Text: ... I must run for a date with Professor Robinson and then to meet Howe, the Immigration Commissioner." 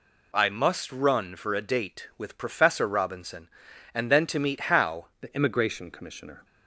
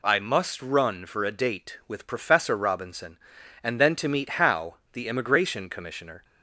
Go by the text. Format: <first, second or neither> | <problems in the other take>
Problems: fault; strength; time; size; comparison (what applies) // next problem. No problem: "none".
second | changes voice at "the"; from 5.1 s on; 1.3 s long